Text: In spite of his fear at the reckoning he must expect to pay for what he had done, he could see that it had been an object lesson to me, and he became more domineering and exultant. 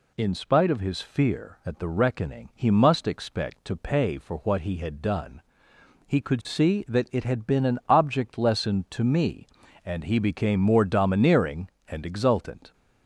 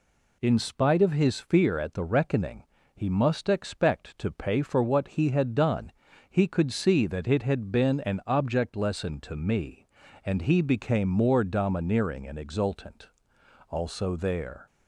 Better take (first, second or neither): first